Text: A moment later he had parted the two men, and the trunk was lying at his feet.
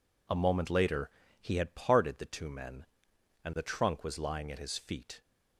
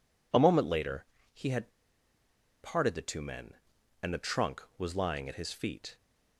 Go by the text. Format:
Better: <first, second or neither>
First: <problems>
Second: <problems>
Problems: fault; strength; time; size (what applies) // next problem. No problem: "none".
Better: first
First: pauses between "later" and "he"; slight; at 1.0 s; 0.30 s long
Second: pauses between "later" and "he"; slight; at 1.0 s; 0.26 s long // pauses between "had" and "parted"; noticeable; at 1.6 s; 0.93 s long